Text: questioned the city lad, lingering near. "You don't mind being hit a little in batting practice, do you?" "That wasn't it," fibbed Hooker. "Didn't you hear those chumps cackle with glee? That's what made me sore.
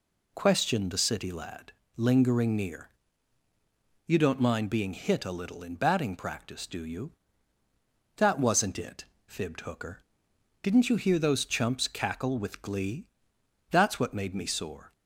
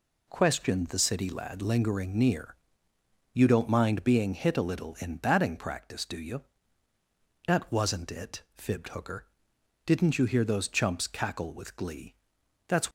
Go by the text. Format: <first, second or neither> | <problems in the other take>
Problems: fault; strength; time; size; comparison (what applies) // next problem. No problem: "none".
first | stops before "what made me sore"; at 12.8 s